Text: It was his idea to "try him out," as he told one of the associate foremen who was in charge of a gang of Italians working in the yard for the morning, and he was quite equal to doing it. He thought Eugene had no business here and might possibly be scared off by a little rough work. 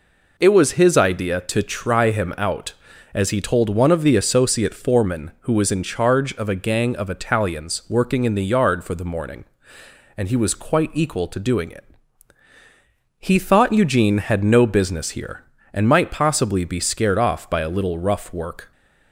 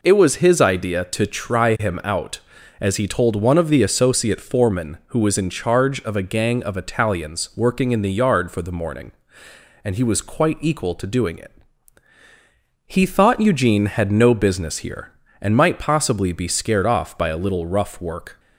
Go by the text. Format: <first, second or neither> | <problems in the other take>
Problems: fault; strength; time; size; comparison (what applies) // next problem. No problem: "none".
neither | none